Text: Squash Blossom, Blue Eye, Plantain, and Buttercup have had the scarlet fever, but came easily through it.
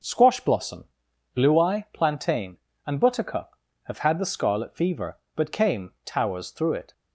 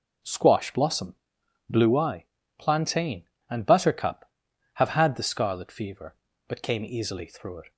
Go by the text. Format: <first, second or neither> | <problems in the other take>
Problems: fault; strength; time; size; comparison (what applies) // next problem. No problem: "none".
second | says "towers" for "easily"; at 6.0 s